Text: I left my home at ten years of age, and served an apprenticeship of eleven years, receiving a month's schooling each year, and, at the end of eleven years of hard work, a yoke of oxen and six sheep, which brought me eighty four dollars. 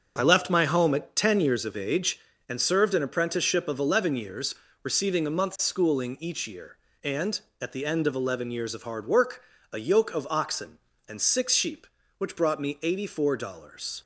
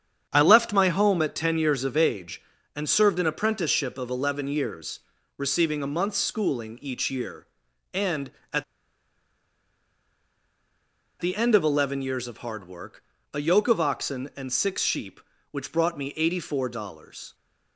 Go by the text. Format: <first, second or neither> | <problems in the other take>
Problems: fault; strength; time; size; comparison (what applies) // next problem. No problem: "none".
first | starts louder than the rest; strong; until 1.3 s; 8 dB; also in the first // pauses between "at" and "the"; strong; at 8.6 s; 2.5 s long